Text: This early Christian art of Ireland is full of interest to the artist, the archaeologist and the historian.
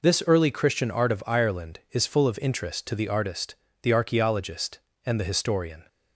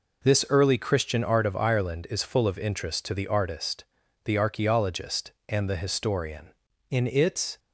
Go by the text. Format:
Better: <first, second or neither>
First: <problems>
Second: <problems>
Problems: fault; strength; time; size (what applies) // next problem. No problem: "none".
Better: first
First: none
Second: goes on to say "In its"; noticeable; from 6.9 s on; 0.68 s long